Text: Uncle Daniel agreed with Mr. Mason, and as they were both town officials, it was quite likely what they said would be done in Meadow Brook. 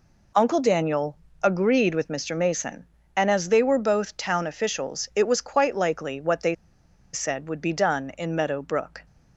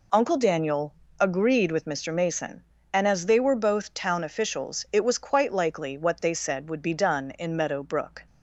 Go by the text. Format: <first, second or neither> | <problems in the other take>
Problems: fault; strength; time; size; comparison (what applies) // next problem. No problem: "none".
second | pauses between "Daniel" and "agreed"; slight; at 1.1 s; 0.28 s long; slight in the second // pauses between "they" and "said"; noticeable; at 6.5 s; 0.58 s long